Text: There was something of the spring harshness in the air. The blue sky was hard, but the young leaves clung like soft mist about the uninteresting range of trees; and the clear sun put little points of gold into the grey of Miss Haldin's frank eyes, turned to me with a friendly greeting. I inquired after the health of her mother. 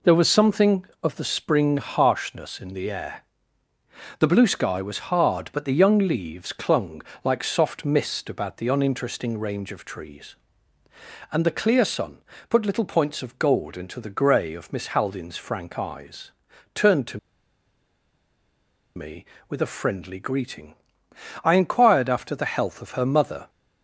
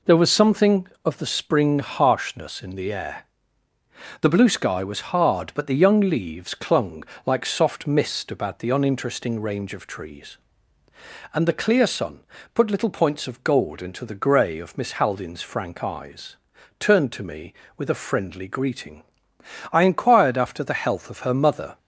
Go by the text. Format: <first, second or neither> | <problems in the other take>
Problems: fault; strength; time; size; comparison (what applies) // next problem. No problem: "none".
second | pauses between "clung" and "like"; slight; at 7.0 s; 0.20 s long; slight in the second // pauses between "sun" and "put"; slight; at 12.2 s; 0.26 s long; slight in the second // pauses between "to" and "me"; strong; at 17.1 s; 1.7 s long